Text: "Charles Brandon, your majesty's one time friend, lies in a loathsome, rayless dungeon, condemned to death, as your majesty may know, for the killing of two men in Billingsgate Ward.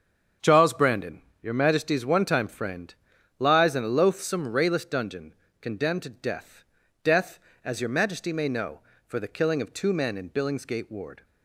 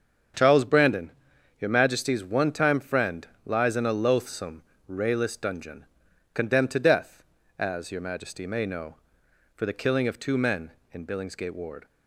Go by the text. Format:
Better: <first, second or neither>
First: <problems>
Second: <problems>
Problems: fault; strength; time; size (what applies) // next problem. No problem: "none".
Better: second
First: starts louder than the rest; strong; until 1.6 s; 7.5 dB // says "death" twice; at 7.0 s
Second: starts louder than the rest; strong; until 1.8 s; 7.5 dB